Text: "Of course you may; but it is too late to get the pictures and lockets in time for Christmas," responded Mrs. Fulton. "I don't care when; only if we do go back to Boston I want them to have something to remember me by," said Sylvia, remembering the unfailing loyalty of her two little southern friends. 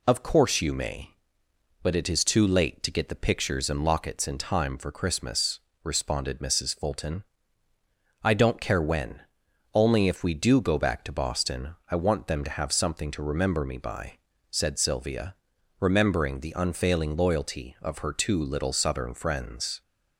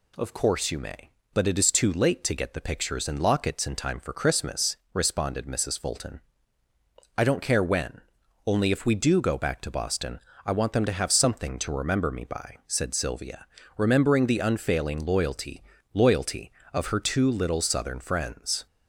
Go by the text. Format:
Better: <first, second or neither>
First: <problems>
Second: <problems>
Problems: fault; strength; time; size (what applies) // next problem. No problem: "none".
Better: first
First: none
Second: pauses between "Boston" and "I"; slight; at 10.1 s; 0.26 s long // says "loyalty" twice; at 15.9 s